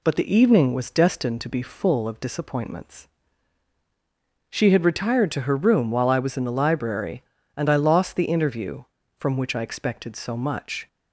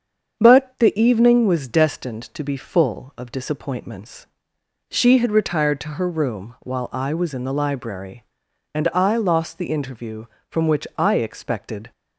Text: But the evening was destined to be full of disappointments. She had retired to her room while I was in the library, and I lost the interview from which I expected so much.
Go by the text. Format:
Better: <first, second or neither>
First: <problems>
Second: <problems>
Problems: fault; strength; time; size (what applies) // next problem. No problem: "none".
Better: first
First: none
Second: starts louder than the rest; strong; until 1.4 s; 7 dB // stops before "so much"; at 11.9 s